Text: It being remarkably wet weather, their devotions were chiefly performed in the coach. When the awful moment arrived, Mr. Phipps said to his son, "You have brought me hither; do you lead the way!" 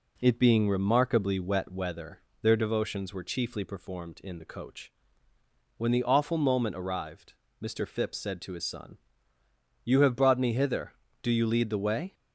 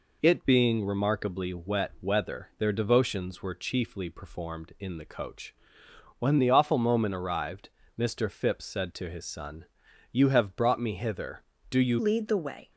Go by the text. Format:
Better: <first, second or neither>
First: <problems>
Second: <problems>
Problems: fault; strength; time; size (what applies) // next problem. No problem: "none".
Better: first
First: none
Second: changes voice at "lead"; from 11.9 s on; 0.8 s long